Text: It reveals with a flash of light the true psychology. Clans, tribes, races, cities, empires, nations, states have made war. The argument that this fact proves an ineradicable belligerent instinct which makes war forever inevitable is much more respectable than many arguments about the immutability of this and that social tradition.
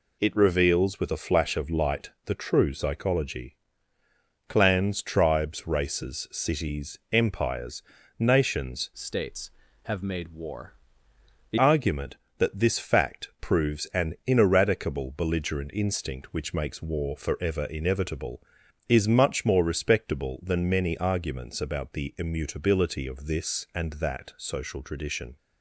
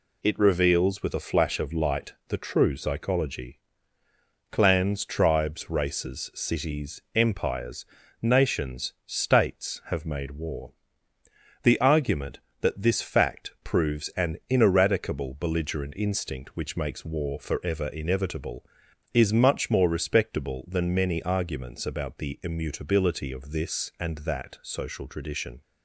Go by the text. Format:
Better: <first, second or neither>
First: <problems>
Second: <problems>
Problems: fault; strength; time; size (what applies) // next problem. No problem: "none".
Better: second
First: pauses between "light" and "the"; slight; at 2.1 s; 0.16 s long // changes voice from "states" to "The"; from 8.9 to 11.5 s; 2.6 s long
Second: pauses between "light" and "the"; slight; at 2.1 s; 0.16 s long